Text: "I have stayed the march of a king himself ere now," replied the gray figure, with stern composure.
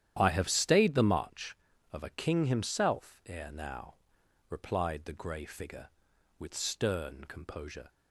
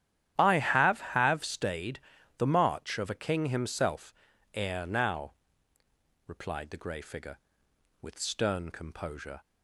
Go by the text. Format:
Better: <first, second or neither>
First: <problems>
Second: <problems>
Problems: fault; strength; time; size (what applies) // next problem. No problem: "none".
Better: first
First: starts louder than the rest; strong; until 1.2 s; 10.5 dB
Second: starts louder than the rest; strong; until 1.3 s; 10.5 dB // says "have" twice; at 0.9 s // pauses between "stayed" and "the"; slight; at 1.9 s; 0.36 s long // pauses between "himself" and "ere"; at 4.1 s; 0.40 s long